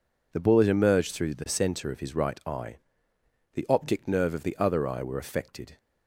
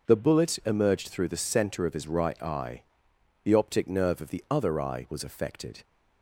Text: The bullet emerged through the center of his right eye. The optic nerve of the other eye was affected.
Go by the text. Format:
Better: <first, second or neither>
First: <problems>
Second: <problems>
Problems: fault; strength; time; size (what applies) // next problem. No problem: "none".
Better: second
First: says "were" for "was"; at 5.0 s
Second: none